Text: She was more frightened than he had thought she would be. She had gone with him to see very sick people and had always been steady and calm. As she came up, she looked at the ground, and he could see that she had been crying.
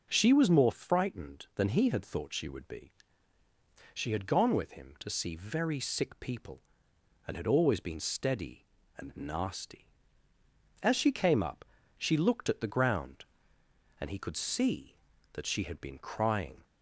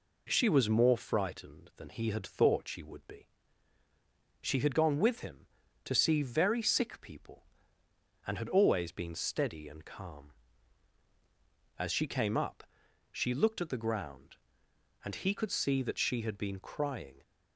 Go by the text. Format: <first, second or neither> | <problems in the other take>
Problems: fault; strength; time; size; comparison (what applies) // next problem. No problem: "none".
second | says "nasty" for "calm"; at 9.1 s